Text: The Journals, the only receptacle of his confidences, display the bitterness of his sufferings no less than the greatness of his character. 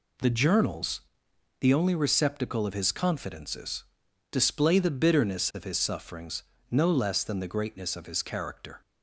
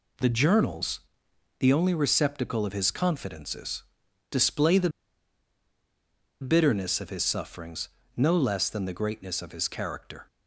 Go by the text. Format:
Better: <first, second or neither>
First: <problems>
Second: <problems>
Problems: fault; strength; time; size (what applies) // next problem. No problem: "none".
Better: first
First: pauses between "sufferings" and "no"; slight; at 6.4 s; 0.26 s long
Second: pauses between "the" and "bitterness"; strong; at 4.8 s; 1.5 s long // pauses between "sufferings" and "no"; slight; at 7.8 s; 0.26 s long